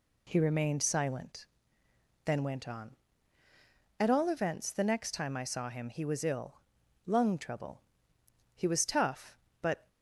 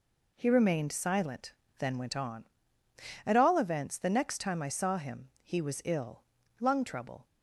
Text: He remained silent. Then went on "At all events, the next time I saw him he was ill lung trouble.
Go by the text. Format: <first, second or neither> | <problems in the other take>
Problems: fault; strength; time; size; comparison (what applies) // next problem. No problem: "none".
second | pauses between "ill" and "lung"; noticeable; at 6.5 s; 0.46 s long; also in the second // goes on to say "He was tough but"; noticeable; from 8.5 s on; 1.3 s long